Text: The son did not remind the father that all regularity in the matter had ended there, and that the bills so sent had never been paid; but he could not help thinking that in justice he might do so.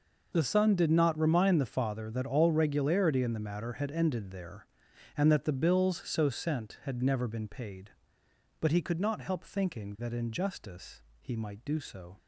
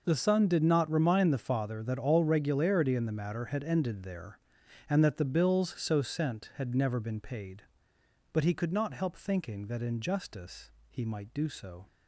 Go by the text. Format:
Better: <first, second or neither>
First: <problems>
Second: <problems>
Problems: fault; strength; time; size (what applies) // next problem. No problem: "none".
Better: neither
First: pauses between "justice" and "he"; slight; at 11.0 s; 0.20 s long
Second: pauses between "justice" and "he"; slight; at 10.7 s; 0.20 s long